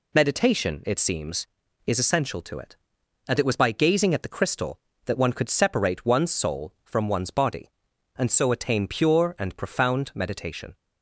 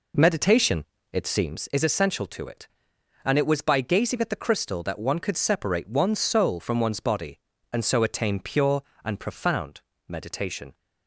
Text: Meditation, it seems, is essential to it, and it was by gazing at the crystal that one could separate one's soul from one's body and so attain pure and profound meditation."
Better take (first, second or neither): first